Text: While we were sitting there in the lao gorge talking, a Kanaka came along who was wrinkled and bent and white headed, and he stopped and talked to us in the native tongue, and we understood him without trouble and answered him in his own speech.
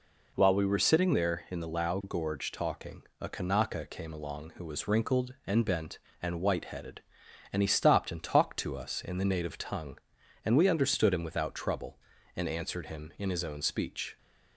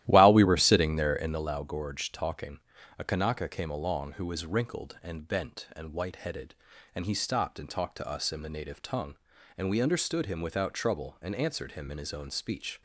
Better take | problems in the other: first | starts louder than the rest; strong; until 1.5 s; 13.5 dB

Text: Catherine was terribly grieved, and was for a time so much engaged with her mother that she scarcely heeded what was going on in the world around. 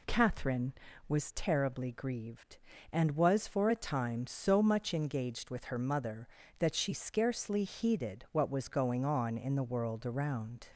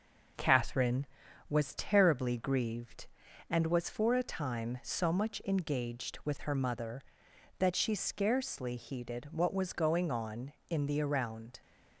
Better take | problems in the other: first | skips "world"; at 11.0 s

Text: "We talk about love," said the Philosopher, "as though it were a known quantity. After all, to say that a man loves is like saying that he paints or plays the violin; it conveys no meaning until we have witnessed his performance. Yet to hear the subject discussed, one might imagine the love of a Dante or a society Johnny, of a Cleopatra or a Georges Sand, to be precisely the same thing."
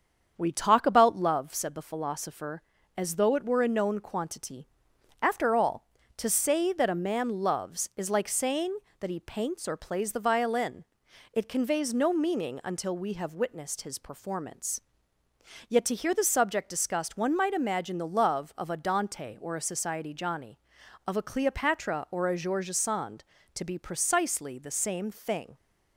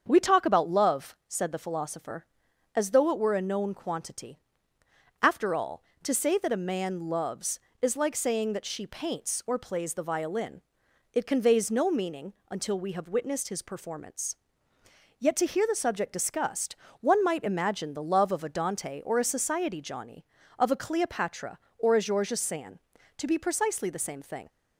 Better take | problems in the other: first | starts louder than the rest; strong; until 1.0 s; 7.5 dB; strong in the first // says "she" for "he"; at 8.6 s // pauses between "meaning" and "until"; slight; at 12.3 s; 0.16 s long

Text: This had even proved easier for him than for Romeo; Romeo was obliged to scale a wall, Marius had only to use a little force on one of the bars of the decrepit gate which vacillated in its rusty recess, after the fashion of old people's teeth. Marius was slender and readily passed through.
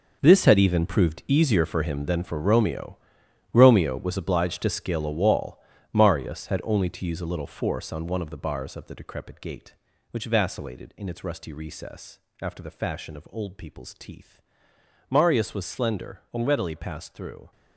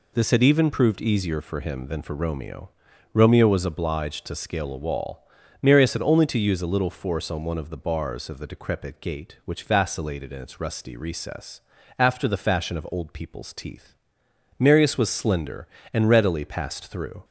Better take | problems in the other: second | gets quieter; strong; throughout; 13 dB

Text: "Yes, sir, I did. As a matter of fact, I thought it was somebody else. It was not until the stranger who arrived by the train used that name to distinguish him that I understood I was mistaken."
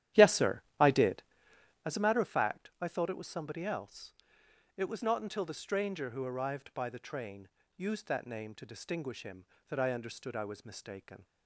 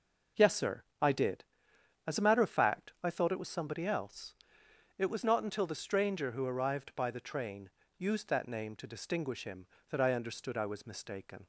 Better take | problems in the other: second | starts louder than the rest; strong; until 2.0 s; 12 dB // pauses between "train" and "used"; slight; at 7.4 s; 0.28 s long; slight in the second

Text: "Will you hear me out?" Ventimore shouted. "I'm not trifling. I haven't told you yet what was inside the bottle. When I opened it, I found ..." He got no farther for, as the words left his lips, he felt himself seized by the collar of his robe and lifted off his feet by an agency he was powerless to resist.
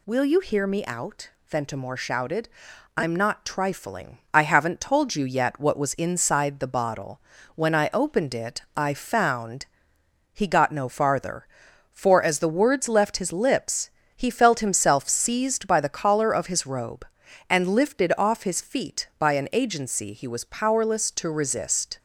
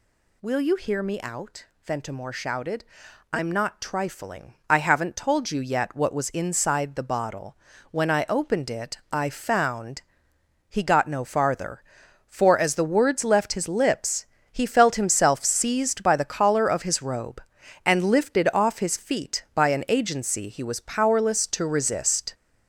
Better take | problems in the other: first | gets louder; noticeable; throughout; 5.5 dB

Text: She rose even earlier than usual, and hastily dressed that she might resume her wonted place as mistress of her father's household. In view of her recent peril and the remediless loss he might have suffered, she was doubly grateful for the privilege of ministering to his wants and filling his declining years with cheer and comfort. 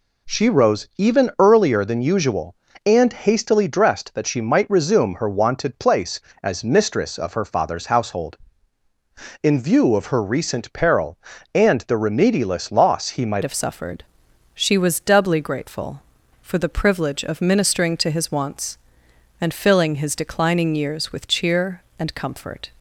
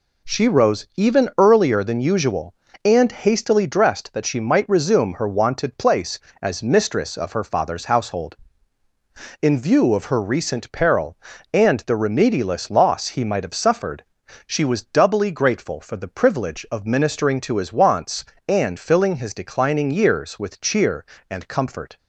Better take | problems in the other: second | changes voice at "have"; from 13.4 s on; 9.2 s long

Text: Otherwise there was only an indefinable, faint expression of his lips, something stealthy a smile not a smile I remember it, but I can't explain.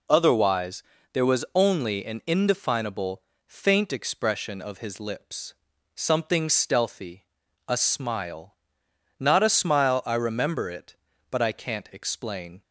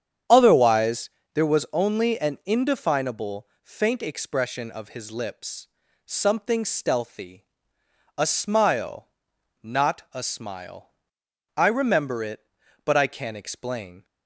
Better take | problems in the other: first | starts louder than the rest; strong; until 1.3 s; 8.5 dB // pauses between "Otherwise" and "there"; slight; at 1.0 s; 0.26 s long; slight in the first // pauses between "stealthy" and "a"; noticeable; at 7.4 s; 0.70 s long; also in the first // pauses between "smile" and "not"; noticeable; at 9.0 s; 0.56 s long; noticeable in the first // pauses between "smile" and "I"; noticeable; at 10.9 s; 0.66 s long

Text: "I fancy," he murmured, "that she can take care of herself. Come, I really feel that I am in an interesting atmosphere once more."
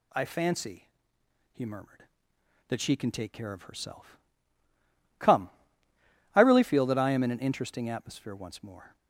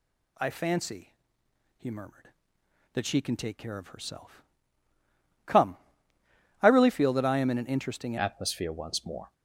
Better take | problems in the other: first | changes voice at "atmosphere"; from 8.1 s on; 1.2 s long

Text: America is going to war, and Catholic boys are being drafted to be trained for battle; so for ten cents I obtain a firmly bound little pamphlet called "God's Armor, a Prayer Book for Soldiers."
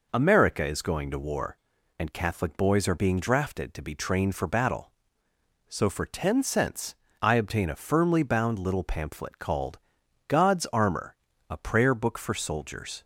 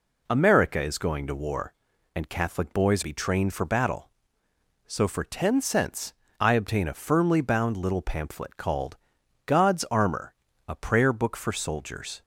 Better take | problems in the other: first | skips "are being drafted to"; at 3.0 s // pauses between "cents" and "I"; slight; at 6.1 s; 0.26 s long; slight in the first // pauses between "called" and "God's"; noticeable; at 8.9 s; 0.50 s long; noticeable in the first

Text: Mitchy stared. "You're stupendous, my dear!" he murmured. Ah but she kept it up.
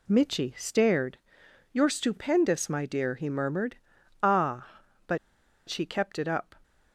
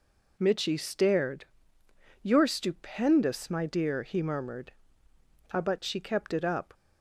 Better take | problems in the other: second | pauses between "but" and "she"; noticeable; at 5.1 s; 0.50 s long

